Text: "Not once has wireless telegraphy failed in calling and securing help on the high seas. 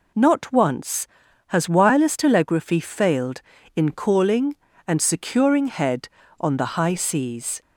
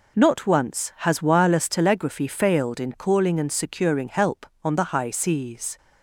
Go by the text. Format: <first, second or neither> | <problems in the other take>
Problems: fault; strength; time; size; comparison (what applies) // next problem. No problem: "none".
second | says "head" for "help"; at 5.6 s